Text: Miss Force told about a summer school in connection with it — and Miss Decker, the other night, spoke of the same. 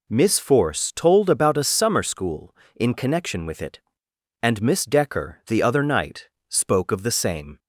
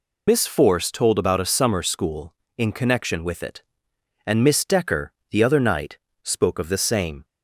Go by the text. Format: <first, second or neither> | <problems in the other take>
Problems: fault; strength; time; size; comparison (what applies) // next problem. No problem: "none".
first | loses the start of "Miss"; at 0.2 s; 70 ms